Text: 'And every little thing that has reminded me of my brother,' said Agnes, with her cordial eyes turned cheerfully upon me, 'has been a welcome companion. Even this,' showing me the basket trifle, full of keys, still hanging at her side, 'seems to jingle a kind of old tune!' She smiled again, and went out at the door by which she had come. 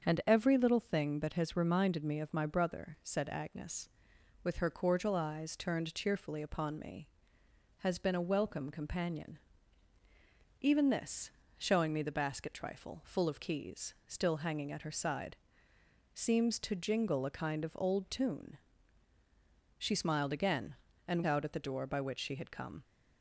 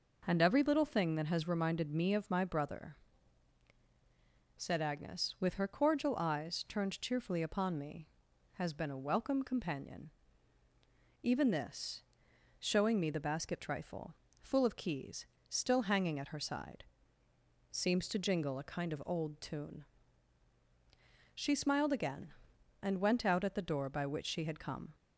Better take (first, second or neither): second